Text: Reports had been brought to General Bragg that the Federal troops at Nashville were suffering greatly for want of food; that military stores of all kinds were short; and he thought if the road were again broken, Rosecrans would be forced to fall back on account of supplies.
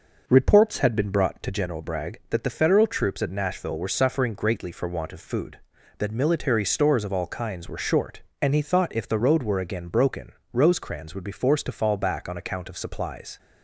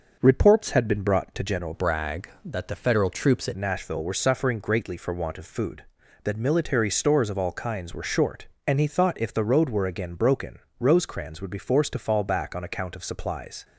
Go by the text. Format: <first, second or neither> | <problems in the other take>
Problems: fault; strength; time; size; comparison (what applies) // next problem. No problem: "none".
first | starts louder than the rest; noticeable; until 1.2 s; 6 dB // changes voice from "Bragg" to "at"; from 1.7 to 3.5 s; 1.8 s long